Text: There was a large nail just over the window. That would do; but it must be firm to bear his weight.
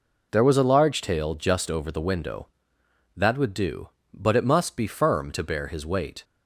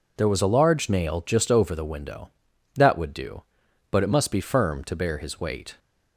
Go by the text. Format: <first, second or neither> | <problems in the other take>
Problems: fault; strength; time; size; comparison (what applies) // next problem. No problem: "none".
second | says "tail" for "nail"; at 1.0 s